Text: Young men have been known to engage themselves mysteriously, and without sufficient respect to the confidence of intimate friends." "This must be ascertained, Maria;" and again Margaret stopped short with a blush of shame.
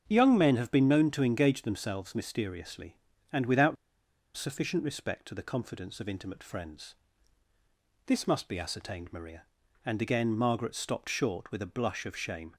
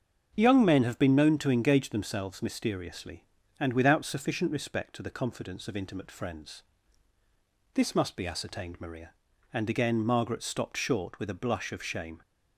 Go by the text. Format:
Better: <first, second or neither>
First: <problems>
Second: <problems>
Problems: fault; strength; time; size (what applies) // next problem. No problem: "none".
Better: second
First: starts louder than the rest; until 1.0 s; 7 dB // pauses between "without" and "sufficient"; noticeable; at 3.7 s; 0.61 s long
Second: starts louder than the rest; until 1.3 s; 7 dB